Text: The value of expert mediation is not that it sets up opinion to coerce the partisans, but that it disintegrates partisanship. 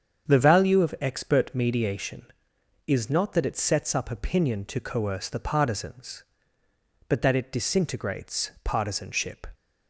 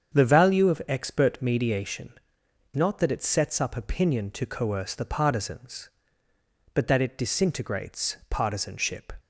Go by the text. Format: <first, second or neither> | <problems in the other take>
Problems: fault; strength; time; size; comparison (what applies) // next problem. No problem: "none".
first | starts louder than the rest; strong; until 1.1 s; 7.5 dB; strong in the first // skips "is"; at 2.4 s